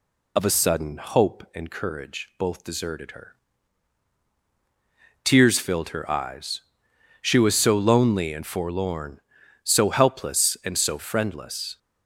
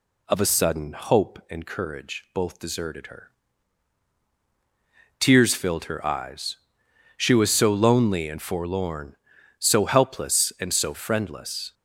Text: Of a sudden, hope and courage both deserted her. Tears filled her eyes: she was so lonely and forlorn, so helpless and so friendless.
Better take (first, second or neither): second